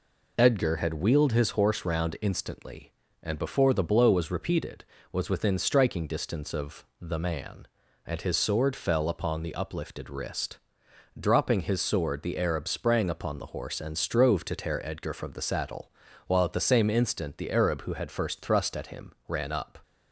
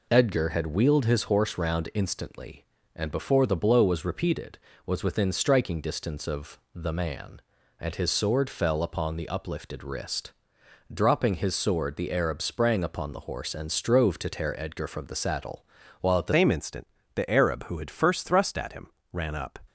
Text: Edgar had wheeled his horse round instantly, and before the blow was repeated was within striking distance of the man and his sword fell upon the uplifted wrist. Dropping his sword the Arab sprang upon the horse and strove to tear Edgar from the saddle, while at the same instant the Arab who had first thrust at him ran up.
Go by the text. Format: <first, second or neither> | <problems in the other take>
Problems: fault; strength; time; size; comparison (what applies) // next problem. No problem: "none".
first | pauses between "of" and "the"; slight; at 6.5 s; 0.16 s long; slight in the first // changes voice at "same"; from 16.3 s on; 3.2 s long // pauses between "instant" and "the"; slight; at 16.8 s; 0.30 s long // pauses between "him" and "ran"; slight; at 18.8 s; 0.24 s long